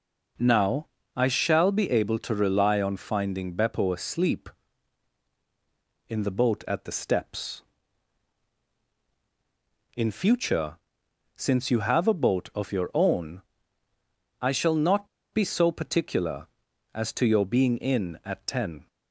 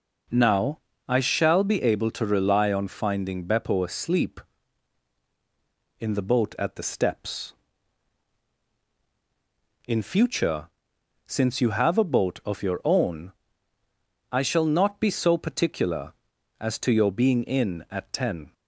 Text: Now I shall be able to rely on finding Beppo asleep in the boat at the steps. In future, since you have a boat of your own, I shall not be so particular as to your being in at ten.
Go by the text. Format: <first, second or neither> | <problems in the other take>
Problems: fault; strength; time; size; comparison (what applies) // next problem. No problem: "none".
second | pauses between "Now" and "I"; slight; at 0.8 s; 0.28 s long; slight in the second // pauses between "not" and "be"; slight; at 15.0 s; 0.25 s long